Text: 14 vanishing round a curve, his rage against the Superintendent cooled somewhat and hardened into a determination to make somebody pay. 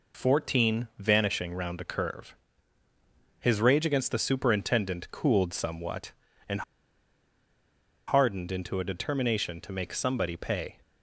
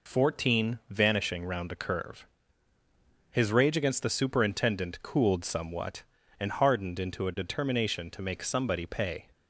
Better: second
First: pauses between "and" and "hardened"; strong; at 6.6 s; 1.4 s long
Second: none

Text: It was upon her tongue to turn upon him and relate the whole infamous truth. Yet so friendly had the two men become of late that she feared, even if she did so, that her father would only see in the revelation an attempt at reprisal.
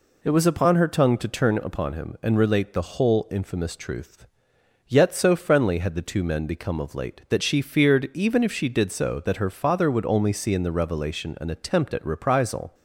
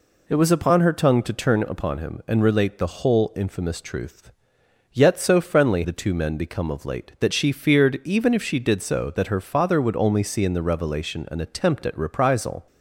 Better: first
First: none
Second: skips "had"; at 5.8 s

